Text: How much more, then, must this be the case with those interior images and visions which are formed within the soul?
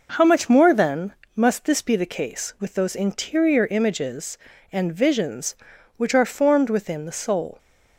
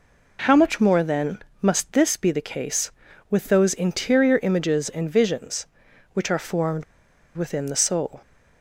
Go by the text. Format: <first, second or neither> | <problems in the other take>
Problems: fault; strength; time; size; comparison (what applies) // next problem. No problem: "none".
first | pauses between "formed" and "within"; noticeable; at 6.8 s; 0.52 s long